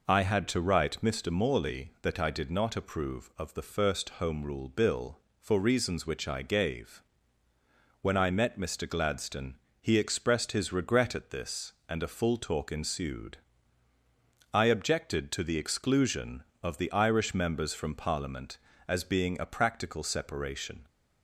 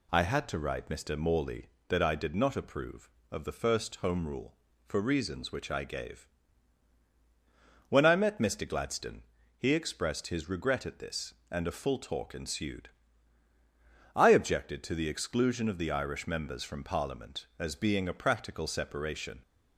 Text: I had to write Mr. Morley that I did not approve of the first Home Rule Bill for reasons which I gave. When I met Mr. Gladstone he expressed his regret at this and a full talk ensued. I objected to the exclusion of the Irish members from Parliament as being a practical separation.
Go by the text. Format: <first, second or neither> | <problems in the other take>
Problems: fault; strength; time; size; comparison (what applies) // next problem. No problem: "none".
first | skips "Bill"; at 4.7 s // pauses between "Gladstone" and "he"; slight; at 9.2 s; 0.34 s long; slight in the first